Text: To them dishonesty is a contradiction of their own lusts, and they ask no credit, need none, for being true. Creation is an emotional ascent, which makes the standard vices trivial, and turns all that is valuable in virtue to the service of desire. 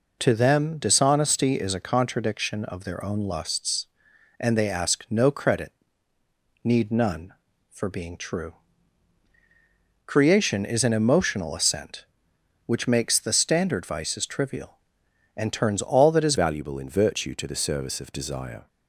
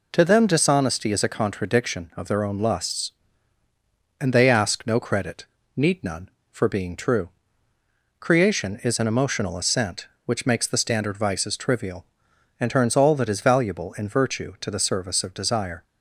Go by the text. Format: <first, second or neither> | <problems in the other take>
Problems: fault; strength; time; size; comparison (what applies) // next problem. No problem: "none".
second | changes voice at "valuable"; from 16.3 s on; 2.3 s long